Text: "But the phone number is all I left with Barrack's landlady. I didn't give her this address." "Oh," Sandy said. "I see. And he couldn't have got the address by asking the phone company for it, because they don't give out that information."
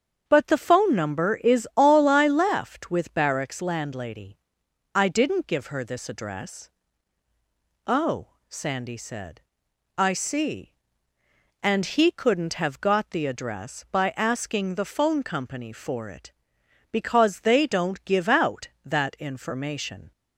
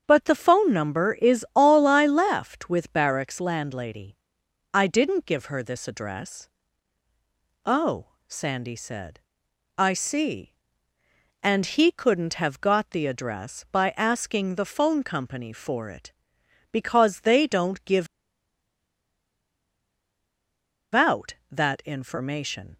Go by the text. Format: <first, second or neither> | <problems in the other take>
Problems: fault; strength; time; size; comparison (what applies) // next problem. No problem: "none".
first | starts louder than the rest; strong; until 1.0 s; 7.5 dB; strong in the first // pauses between "give" and "out"; strong; at 18.0 s; 2.8 s long